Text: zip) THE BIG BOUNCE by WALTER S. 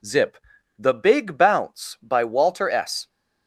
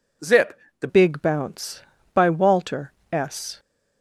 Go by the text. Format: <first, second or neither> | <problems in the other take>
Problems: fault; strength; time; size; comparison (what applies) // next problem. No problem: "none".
first | changes voice at "BIG"; from 0.8 s on; 2.7 s long // pauses between "WALTER" and "S"; slight; at 2.9 s; 0.18 s long